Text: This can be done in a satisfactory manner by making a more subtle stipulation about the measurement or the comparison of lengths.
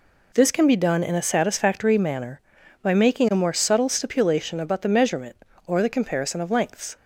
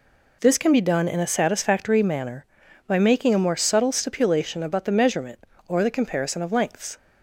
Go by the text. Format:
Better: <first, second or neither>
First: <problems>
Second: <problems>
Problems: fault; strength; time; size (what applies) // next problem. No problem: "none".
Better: neither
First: none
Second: none